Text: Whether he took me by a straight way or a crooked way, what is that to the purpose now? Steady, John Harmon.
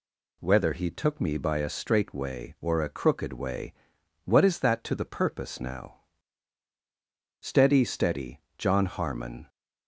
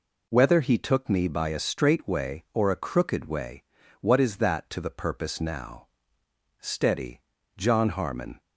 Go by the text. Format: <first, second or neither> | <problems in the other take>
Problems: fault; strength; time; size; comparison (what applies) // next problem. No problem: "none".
second | says "Steady" twice; at 7.8 s